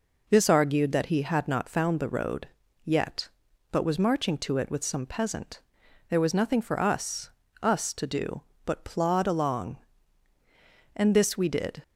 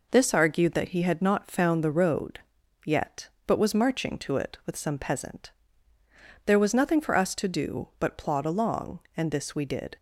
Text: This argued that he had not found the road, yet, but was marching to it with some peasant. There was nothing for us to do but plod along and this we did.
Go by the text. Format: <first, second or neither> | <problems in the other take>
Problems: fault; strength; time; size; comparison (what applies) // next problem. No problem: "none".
second | says "us" twice; at 7.6 s